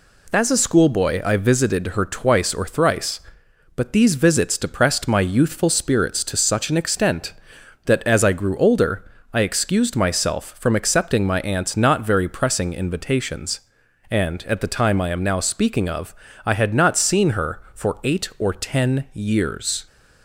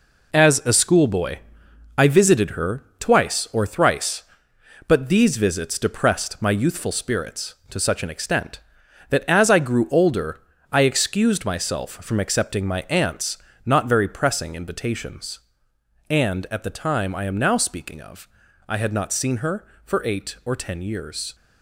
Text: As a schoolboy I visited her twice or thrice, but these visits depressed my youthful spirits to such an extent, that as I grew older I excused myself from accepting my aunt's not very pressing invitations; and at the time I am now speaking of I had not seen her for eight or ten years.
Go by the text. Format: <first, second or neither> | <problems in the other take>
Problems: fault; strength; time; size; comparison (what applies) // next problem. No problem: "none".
first | gets quieter; strong; throughout; 8 dB // pauses between "schoolboy" and "I"; noticeable; at 1.3 s; 0.58 s long // pauses between "her" and "twice"; slight; at 2.8 s; 0.16 s long // pauses between "older" and "I"; slight; at 10.4 s; 0.30 s long; slight in the first // pauses between "aunt's" and "not"; slight; at 13.3 s; 0.28 s long // pauses between "of" and "I"; at 18.2 s; 0.40 s long; slight in the first